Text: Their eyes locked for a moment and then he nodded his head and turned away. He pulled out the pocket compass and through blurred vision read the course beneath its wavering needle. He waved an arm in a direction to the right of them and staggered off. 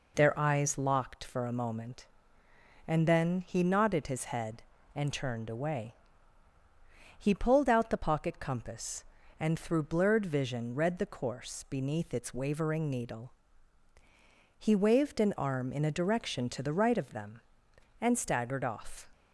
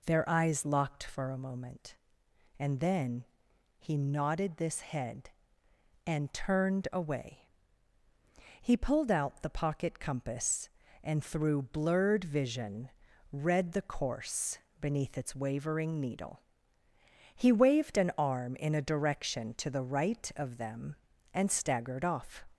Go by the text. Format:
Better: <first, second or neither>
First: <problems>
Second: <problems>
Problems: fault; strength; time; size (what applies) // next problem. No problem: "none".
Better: first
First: none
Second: pauses between "then" and "he"; noticeable; at 3.2 s; 0.56 s long // says "this" for "his"; at 4.5 s // pauses between "vision" and "read"; at 12.8 s; 0.42 s long // pauses between "course" and "beneath"; slight; at 14.5 s; 0.20 s long